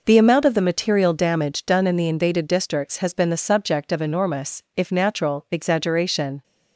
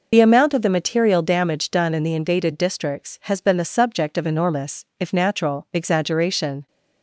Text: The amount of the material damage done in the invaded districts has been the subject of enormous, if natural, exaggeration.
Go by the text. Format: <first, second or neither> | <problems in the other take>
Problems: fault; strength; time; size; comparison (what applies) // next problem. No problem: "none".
first | loses the start of "The"; at 0.1 s; 60 ms